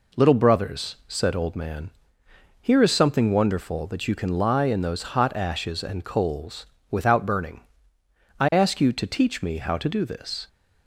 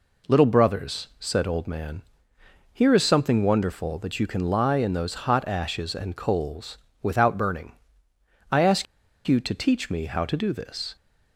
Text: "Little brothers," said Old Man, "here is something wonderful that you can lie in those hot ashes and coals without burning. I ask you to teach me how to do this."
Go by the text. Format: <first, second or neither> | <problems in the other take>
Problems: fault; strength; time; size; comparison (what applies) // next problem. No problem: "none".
first | pauses between "coals" and "without"; slight; at 6.7 s; 0.24 s long; slight in the first // pauses between "ask" and "you"; at 8.8 s; 0.41 s long